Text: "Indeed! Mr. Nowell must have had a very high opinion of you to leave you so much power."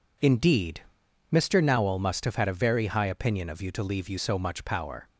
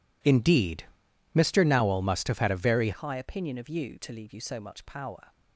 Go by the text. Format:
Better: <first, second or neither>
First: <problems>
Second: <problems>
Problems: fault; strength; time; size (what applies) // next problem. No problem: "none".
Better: first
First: none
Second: changes voice at "high"; from 2.9 s on; 2.4 s long